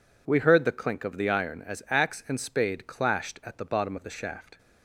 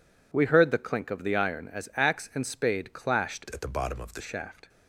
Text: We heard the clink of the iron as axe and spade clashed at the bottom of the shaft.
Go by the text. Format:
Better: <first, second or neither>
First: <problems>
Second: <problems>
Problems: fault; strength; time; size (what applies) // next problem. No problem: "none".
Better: first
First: none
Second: changes voice from "at" to "the"; from 3.5 to 4.2 s; 0.7 s long